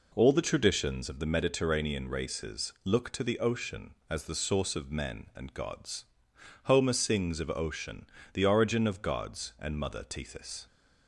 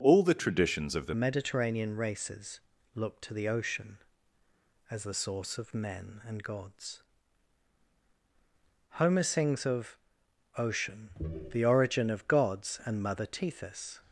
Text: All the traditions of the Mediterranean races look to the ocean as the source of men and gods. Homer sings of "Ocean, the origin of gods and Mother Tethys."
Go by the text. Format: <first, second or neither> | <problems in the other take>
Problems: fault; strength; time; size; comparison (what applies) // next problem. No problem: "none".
first | changes voice at "Mediterranean"; from 1.1 s on; 12.8 s long // pauses between "races" and "look"; slight; at 2.5 s; 0.36 s long // pauses between "of" and "Ocean"; noticeable; at 9.9 s; 0.60 s long